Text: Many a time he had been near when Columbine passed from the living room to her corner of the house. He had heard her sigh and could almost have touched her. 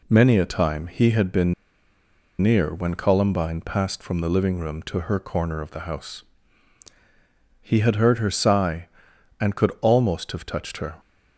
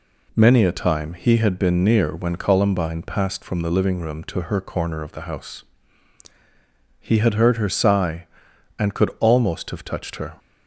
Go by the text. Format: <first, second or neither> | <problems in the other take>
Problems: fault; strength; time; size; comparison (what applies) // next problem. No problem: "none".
second | pauses between "been" and "near"; noticeable; at 1.5 s; 0.86 s long